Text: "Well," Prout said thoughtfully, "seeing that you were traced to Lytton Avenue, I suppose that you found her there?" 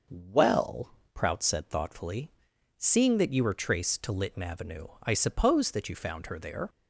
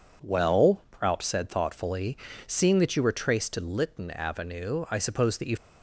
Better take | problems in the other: first | stops before "found her there"; at 5.5 s

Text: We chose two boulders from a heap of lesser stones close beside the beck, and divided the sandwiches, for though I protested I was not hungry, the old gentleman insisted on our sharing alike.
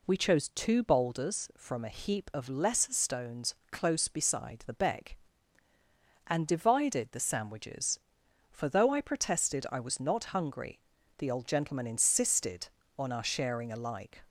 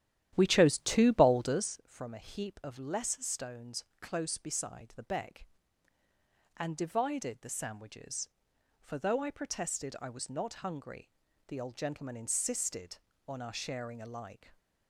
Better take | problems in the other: first | starts louder than the rest; strong; until 1.8 s; 11.5 dB // pauses between "stones" and "close"; slight; at 3.8 s; 0.18 s long; slight in the first

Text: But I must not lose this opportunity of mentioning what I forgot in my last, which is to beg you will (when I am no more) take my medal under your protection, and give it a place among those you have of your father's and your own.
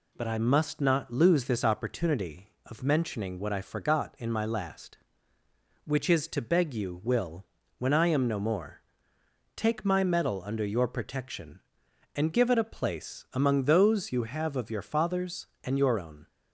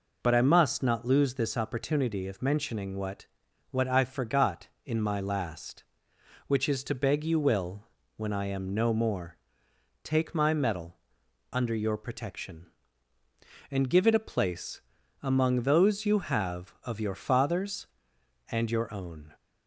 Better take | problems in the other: first | says "what" twice; at 3.7 s // pauses between "medal" and "under"; noticeable; at 10.9 s; 0.52 s long // pauses between "place" and "among"; at 14.8 s; 0.42 s long

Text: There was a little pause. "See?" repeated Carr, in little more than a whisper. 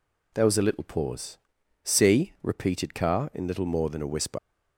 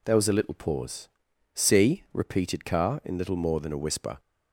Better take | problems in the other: second | leaves "whisper" unfinished; at 4.3 s; 100 ms

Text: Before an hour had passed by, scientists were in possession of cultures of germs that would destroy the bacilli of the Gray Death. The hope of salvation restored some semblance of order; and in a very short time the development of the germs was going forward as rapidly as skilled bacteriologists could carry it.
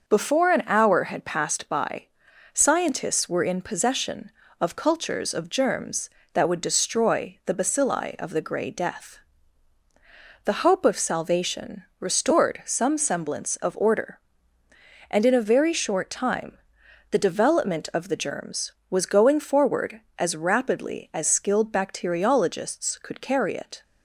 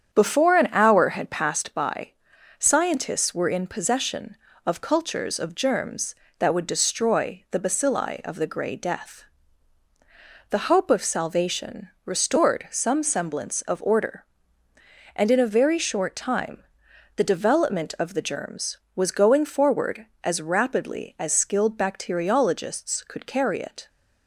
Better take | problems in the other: first | starts louder than the rest; strong; until 1.6 s; 8 dB // pauses between "salvation" and "restored"; slight; at 11.8 s; 0.16 s long; slight in the first // pauses between "time" and "the"; noticeable; at 16.6 s; 0.54 s long; noticeable in the first

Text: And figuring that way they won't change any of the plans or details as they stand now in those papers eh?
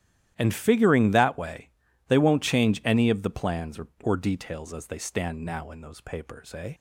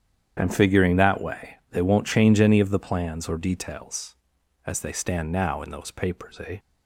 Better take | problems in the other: second | starts louder than the rest; strong; until 1.3 s; 12 dB; strong in the second // pauses between "way" and "they"; at 1.7 s; 0.38 s long; slight in the second // says "or" twice; at 4.0 s

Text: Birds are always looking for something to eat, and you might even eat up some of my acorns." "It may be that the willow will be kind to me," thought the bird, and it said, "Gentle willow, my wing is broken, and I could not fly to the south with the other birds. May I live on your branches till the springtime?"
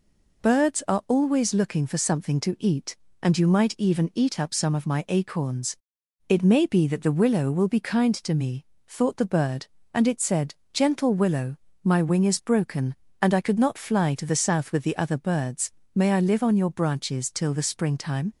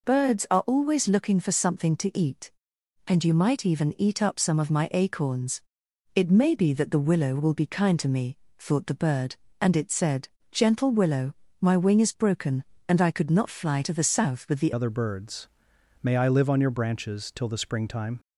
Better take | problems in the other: first | changes voice at "other"; from 14.7 s on; 3.4 s long

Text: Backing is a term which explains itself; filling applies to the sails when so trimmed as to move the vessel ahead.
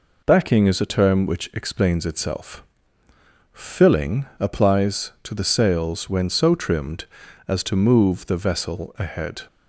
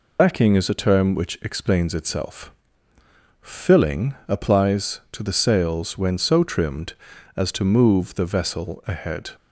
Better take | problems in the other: first | loses the start of "Backing"; at 0.1 s; 65 ms

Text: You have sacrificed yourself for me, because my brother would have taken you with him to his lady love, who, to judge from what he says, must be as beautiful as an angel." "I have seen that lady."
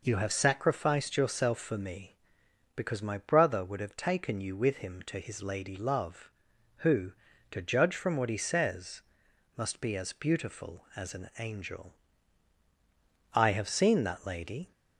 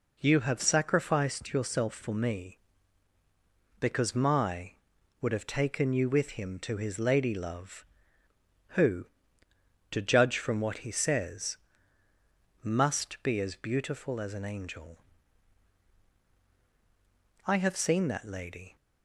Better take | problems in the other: first | skips "brother"; at 4.9 s

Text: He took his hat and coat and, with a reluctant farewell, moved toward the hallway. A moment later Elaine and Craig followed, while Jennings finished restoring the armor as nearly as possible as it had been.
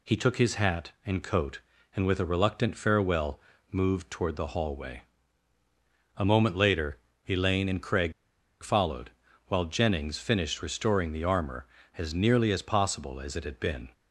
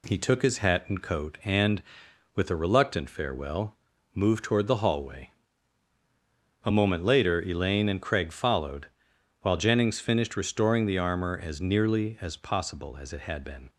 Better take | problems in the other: second | pauses between "later" and "Elaine"; slight; at 6.9 s; 0.30 s long // pauses between "Craig" and "followed"; noticeable; at 8.1 s; 0.51 s long

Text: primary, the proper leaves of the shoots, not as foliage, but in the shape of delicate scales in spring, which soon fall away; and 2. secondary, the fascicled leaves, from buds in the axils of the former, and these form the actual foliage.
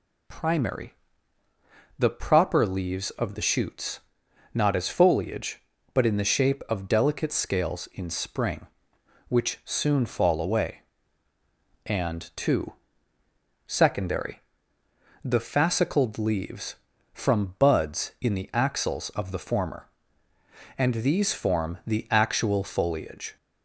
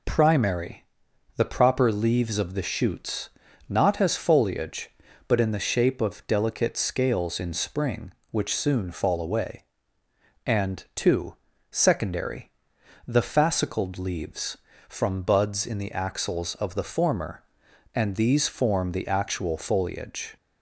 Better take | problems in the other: neither | none

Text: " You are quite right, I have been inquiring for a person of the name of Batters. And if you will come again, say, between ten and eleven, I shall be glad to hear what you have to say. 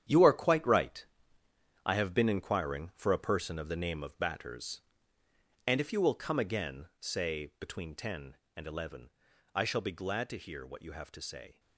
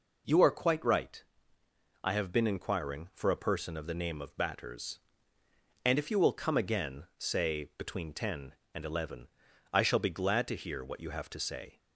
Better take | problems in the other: second | gets quieter; strong; throughout; 11 dB

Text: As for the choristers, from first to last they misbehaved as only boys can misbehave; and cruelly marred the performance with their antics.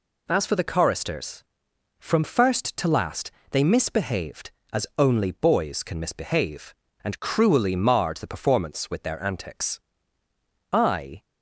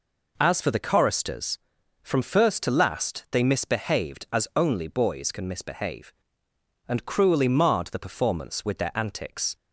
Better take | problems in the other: second | pauses between "last" and "they"; slight; at 3.3 s; 0.20 s long // goes on to say "I"; from 10.7 s on; 0.52 s long

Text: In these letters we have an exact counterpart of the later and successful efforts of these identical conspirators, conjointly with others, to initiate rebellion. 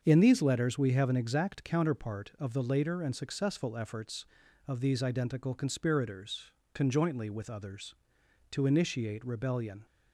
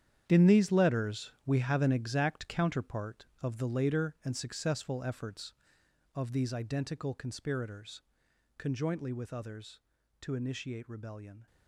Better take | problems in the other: first | gets quieter; strong; throughout; 12.5 dB // starts louder than the rest; strong; until 1.2 s; 9.5 dB; also in the first

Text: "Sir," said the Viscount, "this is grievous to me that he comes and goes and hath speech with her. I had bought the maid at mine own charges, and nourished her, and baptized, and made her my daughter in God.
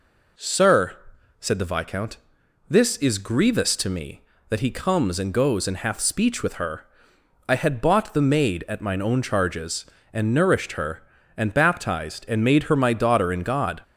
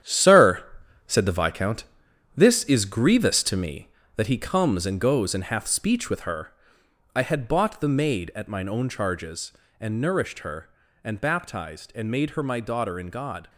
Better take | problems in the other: first | gets quieter; strong; throughout; 9 dB

